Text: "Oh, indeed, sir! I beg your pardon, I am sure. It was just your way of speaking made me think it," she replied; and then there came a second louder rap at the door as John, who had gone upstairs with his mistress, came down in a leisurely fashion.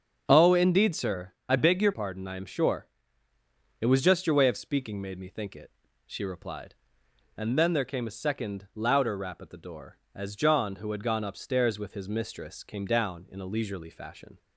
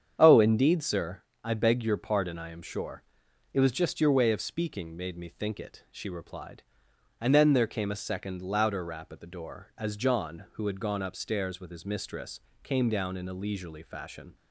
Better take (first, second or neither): second